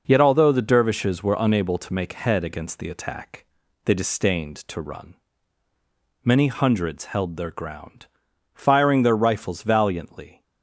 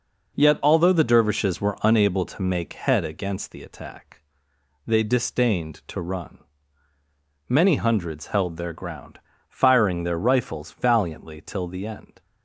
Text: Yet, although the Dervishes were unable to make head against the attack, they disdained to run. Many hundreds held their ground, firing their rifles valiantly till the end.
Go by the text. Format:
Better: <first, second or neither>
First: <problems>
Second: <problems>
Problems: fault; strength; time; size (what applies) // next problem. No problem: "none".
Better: second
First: stops before "till the end"; at 10.4 s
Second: none